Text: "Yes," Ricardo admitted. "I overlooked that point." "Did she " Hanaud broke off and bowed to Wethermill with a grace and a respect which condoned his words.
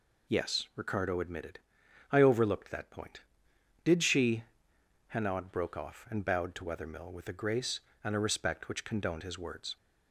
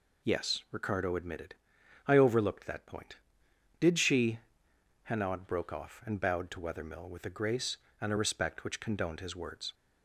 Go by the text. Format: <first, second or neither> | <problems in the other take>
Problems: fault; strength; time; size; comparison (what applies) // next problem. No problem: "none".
neither | none